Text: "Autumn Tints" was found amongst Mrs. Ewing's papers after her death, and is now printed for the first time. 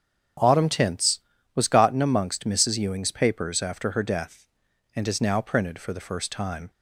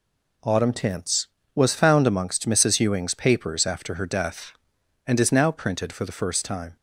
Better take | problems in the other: second | starts louder than the rest; strong; until 1.7 s; 9 dB // says "gotten" for "found"; at 1.6 s

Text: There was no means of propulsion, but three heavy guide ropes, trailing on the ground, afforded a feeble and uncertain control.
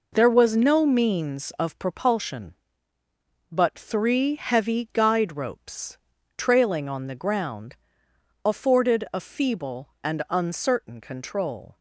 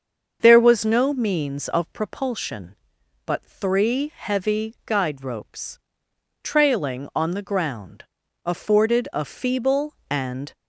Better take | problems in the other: first | starts louder than the rest; until 1.4 s; 6.5 dB // stops before "uncertain control"; at 10.5 s

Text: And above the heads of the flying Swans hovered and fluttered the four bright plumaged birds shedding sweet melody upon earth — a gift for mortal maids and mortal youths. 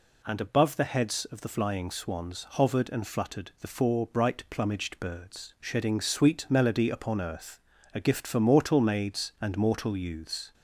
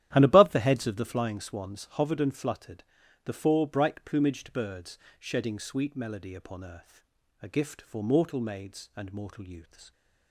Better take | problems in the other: first | starts louder than the rest; strong; until 1.4 s; 12 dB // pauses between "fluttered" and "the"; at 2.8 s; 0.40 s long // pauses between "birds" and "shedding"; slight; at 4.9 s; 0.22 s long

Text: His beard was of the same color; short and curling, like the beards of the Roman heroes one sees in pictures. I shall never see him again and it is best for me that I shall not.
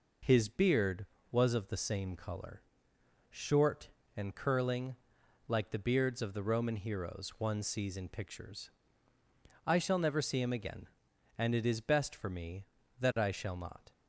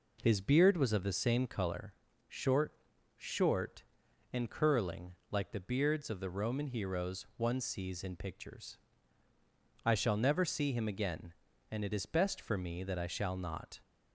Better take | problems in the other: first | says "short" twice; at 3.1 s

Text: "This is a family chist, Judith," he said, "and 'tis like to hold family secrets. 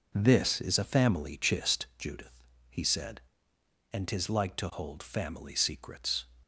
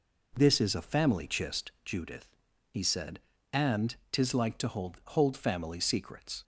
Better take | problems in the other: first | pauses between "and" and "tis"; slight; at 3.9 s; 0.16 s long // says "hold" twice; at 5.0 s

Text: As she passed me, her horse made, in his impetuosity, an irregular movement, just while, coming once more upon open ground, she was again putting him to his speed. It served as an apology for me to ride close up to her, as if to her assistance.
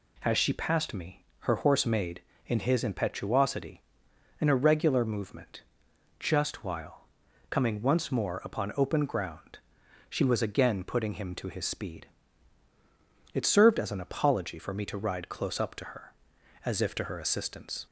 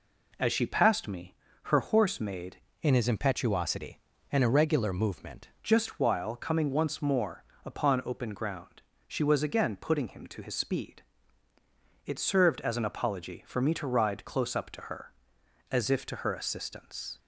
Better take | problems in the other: first | changes voice from "in" to "movement"; from 2.8 to 5.4 s; 2.6 s long // pauses between "more" and "upon"; slight; at 7.4 s; 0.20 s long

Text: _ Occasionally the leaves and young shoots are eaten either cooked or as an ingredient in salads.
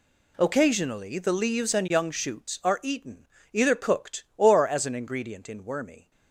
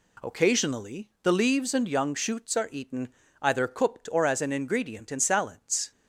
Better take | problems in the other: second | pauses between "eaten" and "either"; slight; at 3.2 s; 0.28 s long; slight in the second // says "wormy" for "salads"; at 5.6 s

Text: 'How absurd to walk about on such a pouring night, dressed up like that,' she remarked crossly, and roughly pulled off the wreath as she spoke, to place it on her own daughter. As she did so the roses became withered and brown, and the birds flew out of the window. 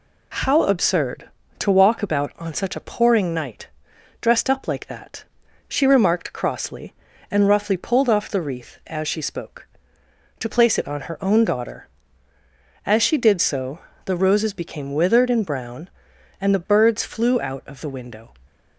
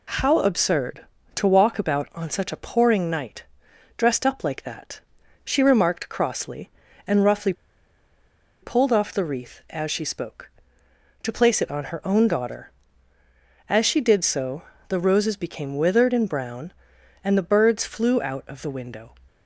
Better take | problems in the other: first | pauses between "roughly" and "pulled"; at 7.5 s; 1.1 s long // pauses between "so" and "the"; slight; at 14.6 s; 0.26 s long; slight in the first

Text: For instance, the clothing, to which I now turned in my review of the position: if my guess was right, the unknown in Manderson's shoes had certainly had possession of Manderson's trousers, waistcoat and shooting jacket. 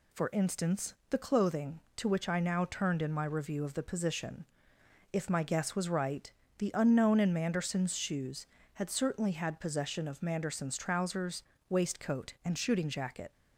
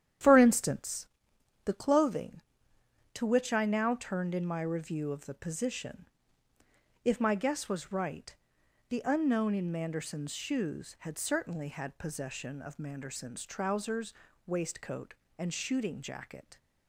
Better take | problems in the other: first | starts louder than the rest; strong; until 1.3 s; 10 dB

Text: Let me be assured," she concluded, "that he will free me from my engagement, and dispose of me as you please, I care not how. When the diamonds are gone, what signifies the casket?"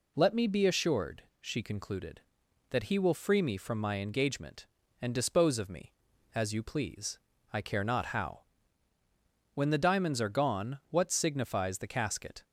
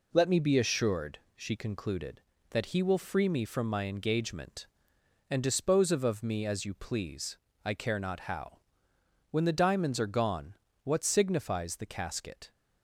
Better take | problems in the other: first | says "of" twice; at 6.0 s

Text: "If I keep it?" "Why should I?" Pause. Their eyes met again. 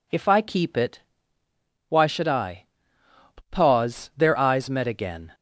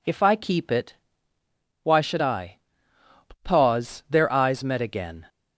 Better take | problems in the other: neither | none

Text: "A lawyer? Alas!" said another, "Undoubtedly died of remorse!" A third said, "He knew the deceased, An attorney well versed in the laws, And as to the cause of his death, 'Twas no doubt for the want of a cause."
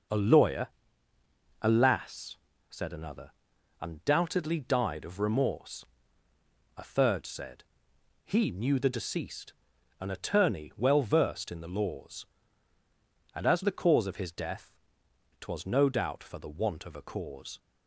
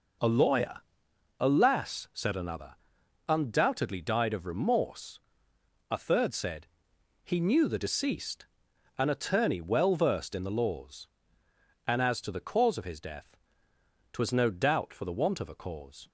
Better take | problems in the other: second | skips "to"; at 13.6 s

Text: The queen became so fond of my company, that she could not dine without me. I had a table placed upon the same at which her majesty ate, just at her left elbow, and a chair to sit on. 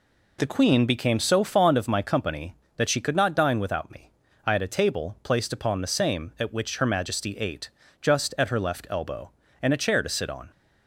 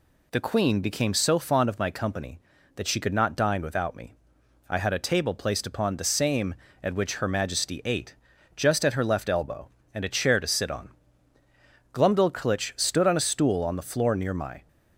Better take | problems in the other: first | goes on to say "Glumdalclitch stood on a stool on the floor near my"; strong; from 11.9 s on; 2.7 s long

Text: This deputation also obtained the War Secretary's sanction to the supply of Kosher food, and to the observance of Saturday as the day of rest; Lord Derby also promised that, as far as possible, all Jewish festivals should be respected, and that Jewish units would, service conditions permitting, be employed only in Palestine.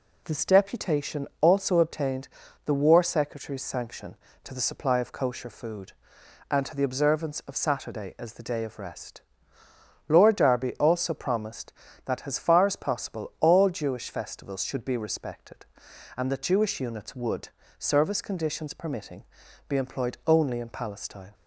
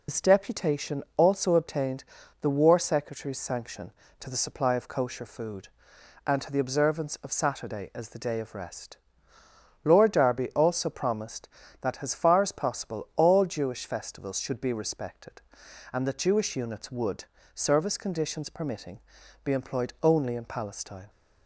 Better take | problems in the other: first | loses the start of "This"; at 0.0 s; 70 ms // pauses between "obtained" and "the"; slight; at 2.0 s; 0.34 s long; slight in the first

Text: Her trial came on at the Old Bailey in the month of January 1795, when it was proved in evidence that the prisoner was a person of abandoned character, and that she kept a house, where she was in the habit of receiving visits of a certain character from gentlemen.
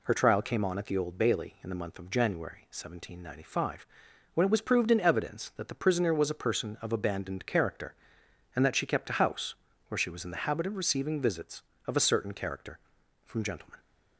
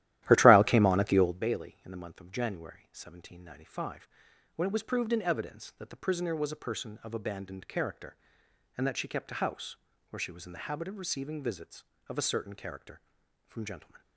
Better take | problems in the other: first | starts louder than the rest; strong; until 1.4 s; 13.5 dB

